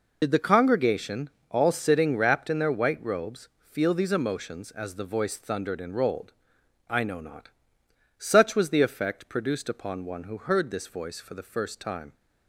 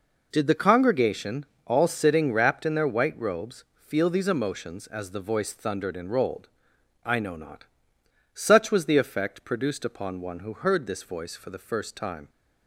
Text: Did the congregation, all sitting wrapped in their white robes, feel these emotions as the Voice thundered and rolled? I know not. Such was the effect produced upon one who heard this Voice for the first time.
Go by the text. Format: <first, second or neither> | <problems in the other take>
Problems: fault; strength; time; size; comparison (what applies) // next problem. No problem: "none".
second | loses the start of "Did"; at 0.2 s; 65 ms